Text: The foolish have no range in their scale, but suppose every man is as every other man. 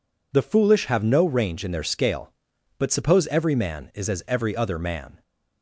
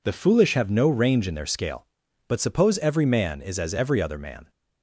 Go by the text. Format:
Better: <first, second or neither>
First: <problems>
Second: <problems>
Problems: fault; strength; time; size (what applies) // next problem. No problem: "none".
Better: neither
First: none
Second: none